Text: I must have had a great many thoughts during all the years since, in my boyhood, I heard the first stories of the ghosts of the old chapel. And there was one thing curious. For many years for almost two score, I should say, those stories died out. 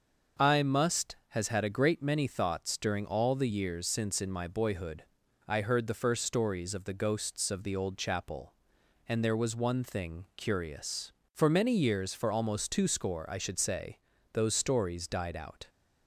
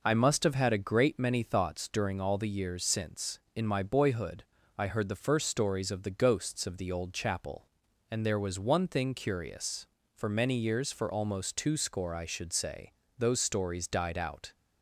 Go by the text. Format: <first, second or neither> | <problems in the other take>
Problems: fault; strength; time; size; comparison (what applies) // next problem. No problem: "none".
second | starts louder than the rest; until 1.5 s; 6 dB // says "has" for "have"; at 1.2 s